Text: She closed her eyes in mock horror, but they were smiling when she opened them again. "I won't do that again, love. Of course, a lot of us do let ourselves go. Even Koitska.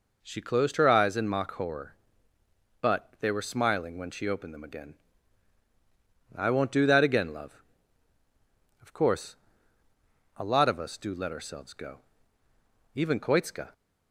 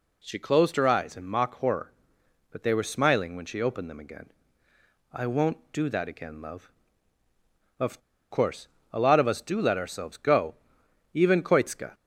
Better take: first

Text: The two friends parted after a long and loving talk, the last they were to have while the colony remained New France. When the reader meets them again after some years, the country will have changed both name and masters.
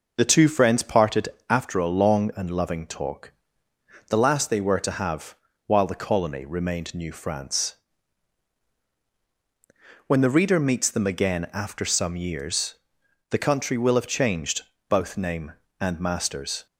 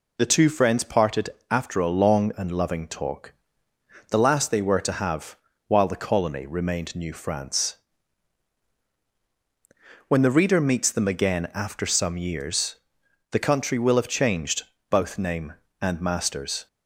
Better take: second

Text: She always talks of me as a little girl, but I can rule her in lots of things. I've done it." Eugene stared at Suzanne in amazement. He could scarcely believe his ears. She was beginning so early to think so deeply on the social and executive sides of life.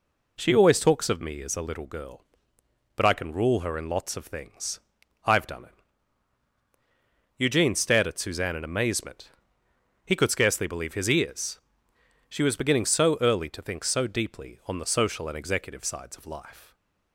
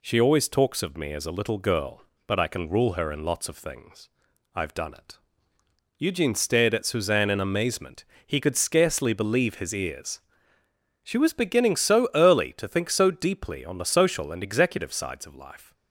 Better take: neither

